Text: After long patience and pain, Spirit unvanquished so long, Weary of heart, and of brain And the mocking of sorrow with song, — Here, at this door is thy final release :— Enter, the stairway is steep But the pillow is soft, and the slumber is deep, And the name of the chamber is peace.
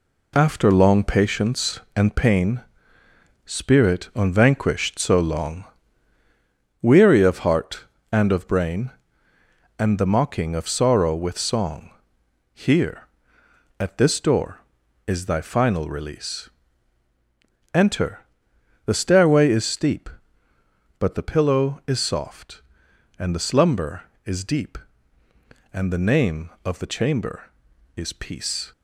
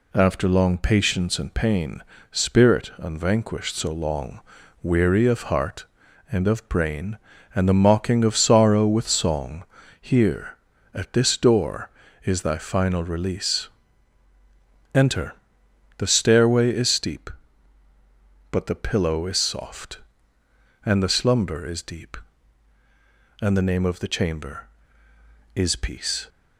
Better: neither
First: none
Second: none

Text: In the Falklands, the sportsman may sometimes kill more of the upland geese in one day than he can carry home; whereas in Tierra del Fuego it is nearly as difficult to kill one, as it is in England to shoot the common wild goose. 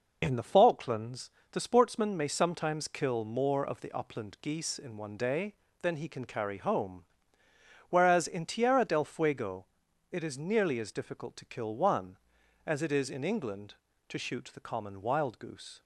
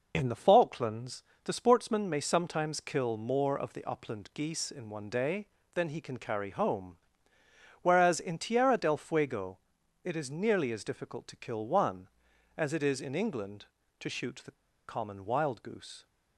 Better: first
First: pauses between "Fuego" and "it"; noticeable; at 9.6 s; 0.46 s long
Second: pauses between "Fuego" and "it"; noticeable; at 9.5 s; 0.46 s long // pauses between "the" and "common"; slight; at 14.5 s; 0.33 s long

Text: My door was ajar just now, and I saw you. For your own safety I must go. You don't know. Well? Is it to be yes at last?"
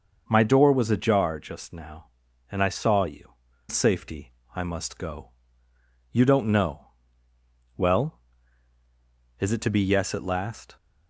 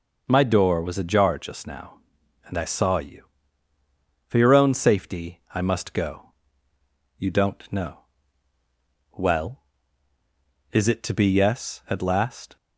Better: second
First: skips "For your own"; at 3.5 s // pauses between "safety" and "I"; slight; at 4.3 s; 0.20 s long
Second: none

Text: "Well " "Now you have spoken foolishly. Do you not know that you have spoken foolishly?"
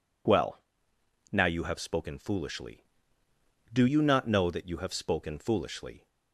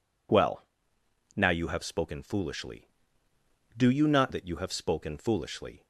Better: first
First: none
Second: skips "know"; at 4.3 s

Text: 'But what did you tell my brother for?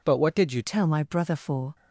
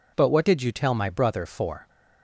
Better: second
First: changes voice at "tell"; from 0.6 s on; 1.1 s long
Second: none

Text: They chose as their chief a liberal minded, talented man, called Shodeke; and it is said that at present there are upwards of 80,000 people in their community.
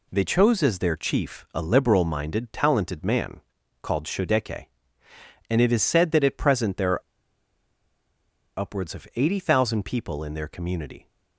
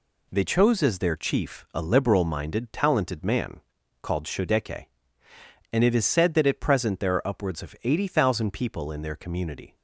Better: second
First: pauses between "are" and "upwards"; strong; at 7.0 s; 1.5 s long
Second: none

